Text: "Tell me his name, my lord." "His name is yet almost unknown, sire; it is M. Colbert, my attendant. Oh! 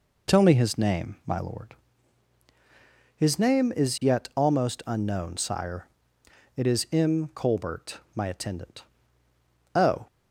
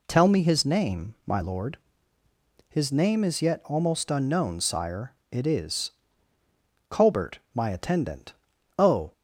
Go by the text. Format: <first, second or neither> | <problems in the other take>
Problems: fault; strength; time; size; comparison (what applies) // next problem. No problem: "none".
first | skips "M"; at 6.4 s